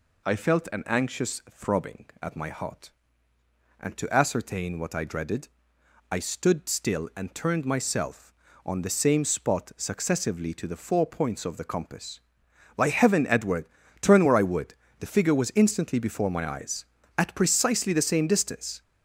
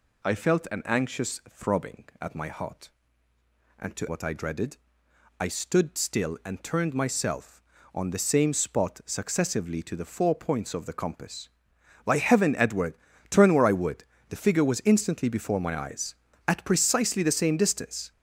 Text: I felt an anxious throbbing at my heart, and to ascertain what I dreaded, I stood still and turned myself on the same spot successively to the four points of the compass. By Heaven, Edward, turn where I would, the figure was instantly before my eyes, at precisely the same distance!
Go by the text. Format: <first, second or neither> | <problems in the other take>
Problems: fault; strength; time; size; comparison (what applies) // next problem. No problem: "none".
first | skips "ascertain"; at 4.0 s